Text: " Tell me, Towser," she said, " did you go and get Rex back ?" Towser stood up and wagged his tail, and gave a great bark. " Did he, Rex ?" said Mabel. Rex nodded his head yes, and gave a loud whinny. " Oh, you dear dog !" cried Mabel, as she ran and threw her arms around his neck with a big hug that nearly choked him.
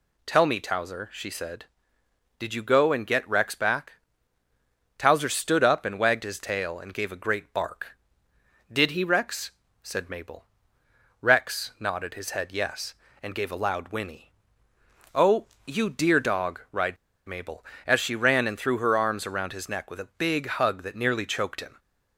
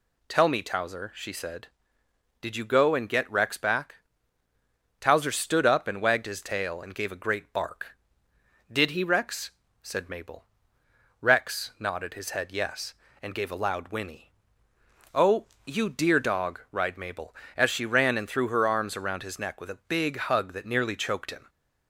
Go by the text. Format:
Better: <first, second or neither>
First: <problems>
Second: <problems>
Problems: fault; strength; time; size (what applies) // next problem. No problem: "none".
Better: second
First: pauses between "cried" and "Mabel"; slight; at 16.9 s; 0.32 s long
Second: none